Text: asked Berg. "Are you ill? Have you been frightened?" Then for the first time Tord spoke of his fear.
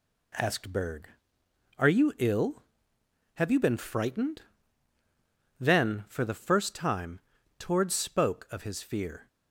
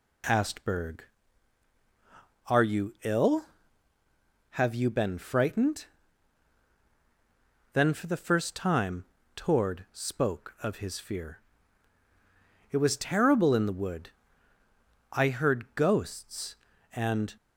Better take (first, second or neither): first